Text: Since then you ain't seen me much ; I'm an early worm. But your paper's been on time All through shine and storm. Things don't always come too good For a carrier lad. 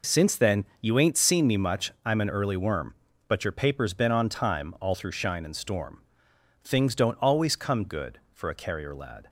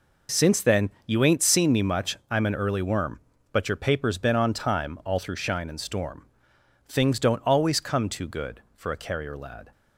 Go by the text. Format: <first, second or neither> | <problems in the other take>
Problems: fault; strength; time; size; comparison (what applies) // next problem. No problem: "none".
second | pauses between "then" and "you"; slight; at 0.6 s; 0.16 s long; slight in the second // skips "too"; at 7.8 s